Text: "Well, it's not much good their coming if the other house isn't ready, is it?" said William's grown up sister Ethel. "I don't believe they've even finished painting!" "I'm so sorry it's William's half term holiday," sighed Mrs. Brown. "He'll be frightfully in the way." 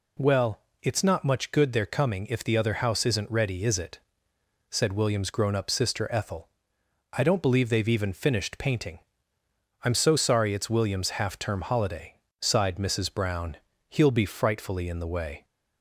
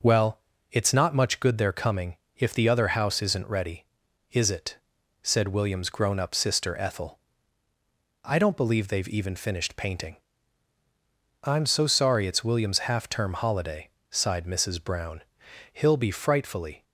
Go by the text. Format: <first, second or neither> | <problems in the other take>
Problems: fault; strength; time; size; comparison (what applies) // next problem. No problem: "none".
first | pauses between "coming" and "if"; slight; at 2.1 s; 0.20 s long // stops before "in the way"; at 16.8 s